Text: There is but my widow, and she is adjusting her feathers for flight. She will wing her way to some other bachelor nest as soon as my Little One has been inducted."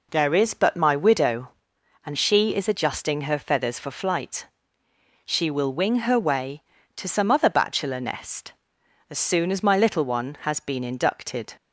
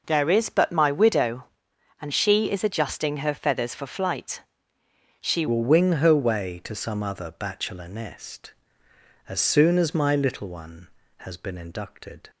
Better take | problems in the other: first | changes voice at "will"; from 5.4 s on; 6.8 s long

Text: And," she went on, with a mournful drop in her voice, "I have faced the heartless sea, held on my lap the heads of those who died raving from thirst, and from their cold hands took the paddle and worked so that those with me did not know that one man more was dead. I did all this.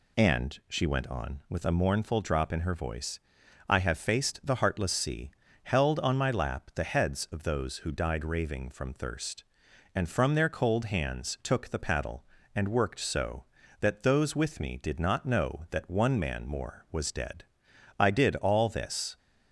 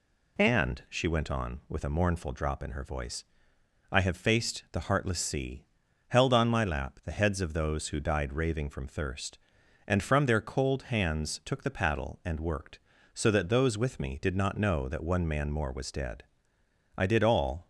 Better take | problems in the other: first | stops before "this"; at 17.6 s

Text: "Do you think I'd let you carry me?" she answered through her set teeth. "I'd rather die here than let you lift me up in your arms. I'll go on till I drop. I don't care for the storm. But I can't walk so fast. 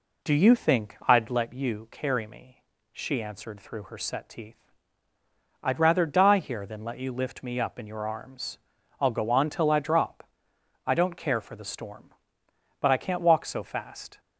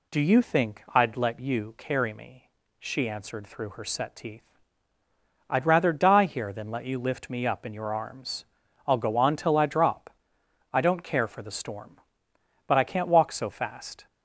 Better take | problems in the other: second | starts louder than the rest; slight; until 1.5 s; 3 dB

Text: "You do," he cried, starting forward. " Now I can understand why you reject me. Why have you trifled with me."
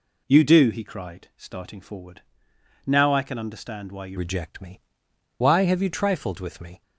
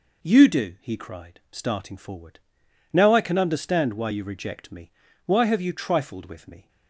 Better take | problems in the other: second | changes voice at "reject"; from 4.1 s on; 2.7 s long

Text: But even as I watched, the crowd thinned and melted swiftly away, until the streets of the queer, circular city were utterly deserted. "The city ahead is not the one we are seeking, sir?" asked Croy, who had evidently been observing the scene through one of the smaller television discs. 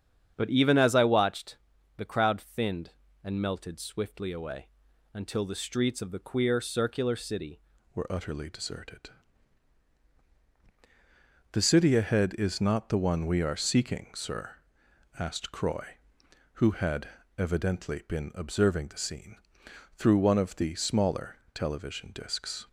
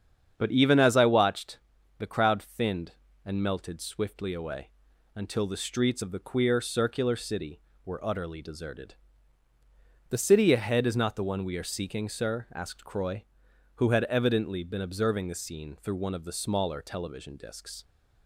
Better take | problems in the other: second | starts louder than the rest; strong; until 1.3 s; 8 dB; strong in the second // changes voice at "were"; from 7.9 s on; 14.7 s long // pauses between "had" and "evidently"; slight; at 17.0 s; 0.28 s long // pauses between "scene" and "through"; noticeable; at 19.3 s; 0.62 s long // pauses between "smaller" and "television"; slight; at 21.3 s; 0.18 s long

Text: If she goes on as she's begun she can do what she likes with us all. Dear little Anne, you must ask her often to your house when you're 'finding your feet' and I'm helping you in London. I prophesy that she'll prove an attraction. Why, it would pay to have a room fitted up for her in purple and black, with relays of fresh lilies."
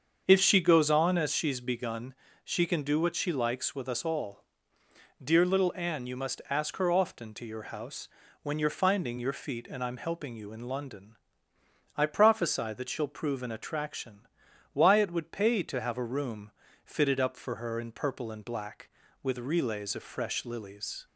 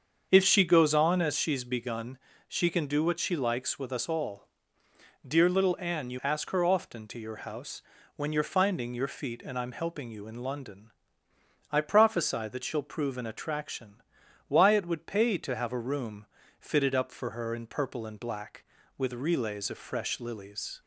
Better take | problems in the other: first | starts louder than the rest; until 1.3 s; 7 dB; also in the first // pauses between "begun" and "she"; slight; at 2.1 s; 0.28 s long; slight in the first // skips "must"; at 6.2 s // pauses between "house" and "when"; slight; at 7.8 s; 0.34 s long; slight in the first // pauses between "room" and "fitted"; slight; at 16.2 s; 0.34 s long; slight in the first

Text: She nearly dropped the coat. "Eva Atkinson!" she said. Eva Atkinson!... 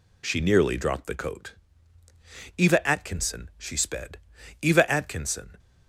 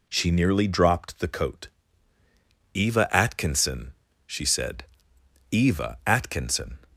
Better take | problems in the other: second | says "sped" for "said"; at 3.7 s

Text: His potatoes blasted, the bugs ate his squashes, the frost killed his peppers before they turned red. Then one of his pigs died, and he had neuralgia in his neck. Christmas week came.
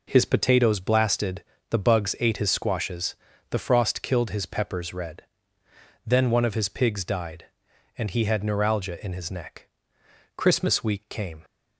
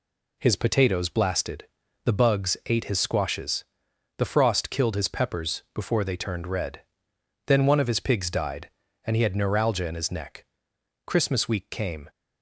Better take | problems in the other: second | skips "before they turned"; at 4.9 s

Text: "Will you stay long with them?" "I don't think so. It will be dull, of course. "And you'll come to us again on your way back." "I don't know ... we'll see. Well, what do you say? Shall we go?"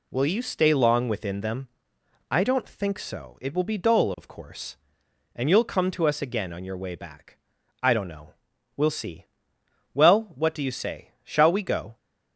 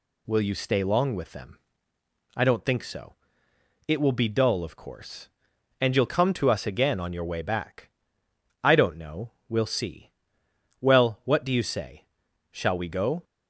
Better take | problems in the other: second | says "within" for "with"; at 1.0 s

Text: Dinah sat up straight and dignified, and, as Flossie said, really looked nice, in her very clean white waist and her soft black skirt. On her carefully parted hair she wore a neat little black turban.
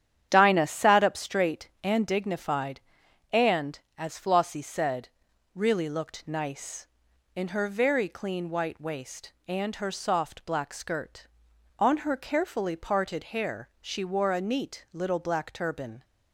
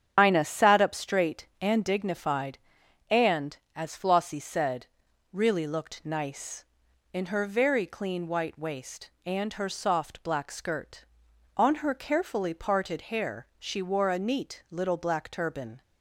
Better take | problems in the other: first | loses the start of "Dinah"; at 0.1 s; 100 ms // starts louder than the rest; strong; until 1.1 s; 8 dB; strong in the first

